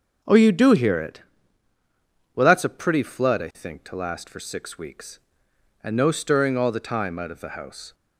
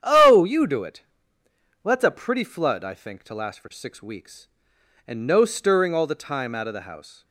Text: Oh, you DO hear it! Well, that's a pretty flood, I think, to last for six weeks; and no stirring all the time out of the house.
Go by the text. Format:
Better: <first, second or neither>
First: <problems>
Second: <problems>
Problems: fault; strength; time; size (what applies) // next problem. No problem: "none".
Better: first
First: none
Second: starts louder than the rest; strong; until 1.0 s; 9 dB // skips "hear"; at 0.8 s